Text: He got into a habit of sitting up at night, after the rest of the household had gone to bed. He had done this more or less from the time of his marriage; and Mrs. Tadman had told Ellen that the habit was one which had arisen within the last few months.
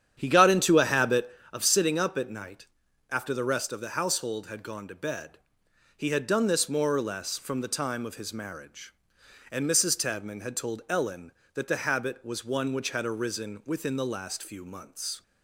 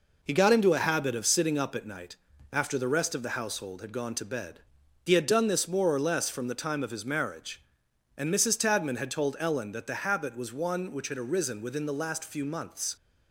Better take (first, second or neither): second